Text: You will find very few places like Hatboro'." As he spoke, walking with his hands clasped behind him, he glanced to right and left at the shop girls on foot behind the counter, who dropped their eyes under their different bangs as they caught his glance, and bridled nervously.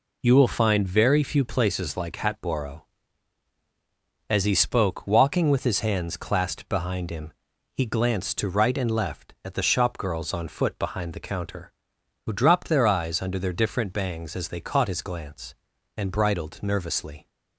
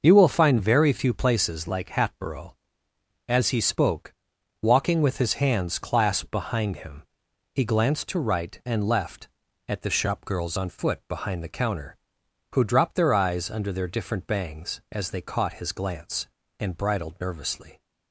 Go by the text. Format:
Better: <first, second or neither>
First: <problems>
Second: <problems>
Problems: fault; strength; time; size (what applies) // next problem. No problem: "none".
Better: neither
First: none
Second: none